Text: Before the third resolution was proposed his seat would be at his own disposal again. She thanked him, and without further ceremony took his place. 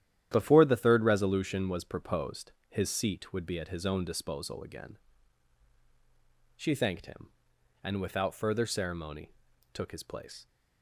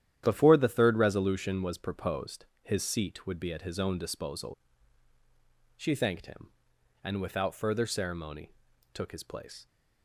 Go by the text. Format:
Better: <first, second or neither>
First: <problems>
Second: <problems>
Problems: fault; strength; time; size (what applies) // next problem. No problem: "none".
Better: first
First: starts louder than the rest; strong; until 1.3 s; 11 dB // pauses between "proposed" and "his"; slight; at 2.5 s; 0.16 s long // pauses between "ceremony" and "took"; at 9.3 s; 0.40 s long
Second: starts louder than the rest; strong; until 1.2 s; 11 dB // pauses between "proposed" and "his"; slight; at 2.4 s; 0.16 s long // skips "again"; at 5.1 s // pauses between "ceremony" and "took"; at 8.5 s; 0.40 s long